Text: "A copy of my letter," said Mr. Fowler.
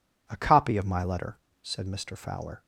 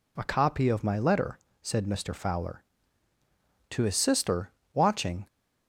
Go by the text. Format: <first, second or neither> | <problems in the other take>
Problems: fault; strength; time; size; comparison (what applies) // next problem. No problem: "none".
first | goes on to say "To his sister watching"; from 3.6 s on; 1.6 s long